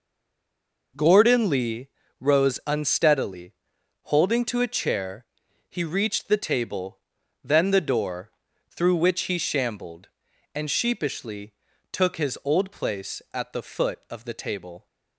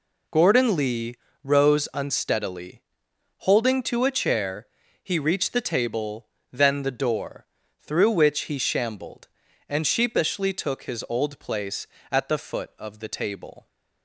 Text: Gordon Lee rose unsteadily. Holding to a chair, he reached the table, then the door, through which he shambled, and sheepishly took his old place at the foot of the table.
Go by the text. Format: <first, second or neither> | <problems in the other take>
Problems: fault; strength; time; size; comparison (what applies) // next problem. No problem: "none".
second | stays silent before the first word; slight; until 0.9 s; 0.9 s long // pauses between "Lee" and "rose"; slight; at 1.8 s; 0.30 s long; slight in the second // pauses between "sheepishly" and "took"; at 11.5 s; 0.40 s long